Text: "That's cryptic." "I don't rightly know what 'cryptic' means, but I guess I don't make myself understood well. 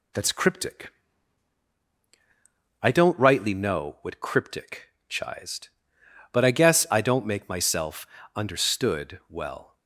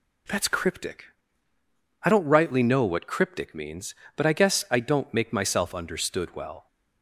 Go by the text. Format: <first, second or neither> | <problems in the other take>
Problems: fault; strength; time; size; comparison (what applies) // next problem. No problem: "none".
second | says "chised" for "means"; at 5.0 s // pauses between "myself" and "understood"; slight; at 8.0 s; 0.28 s long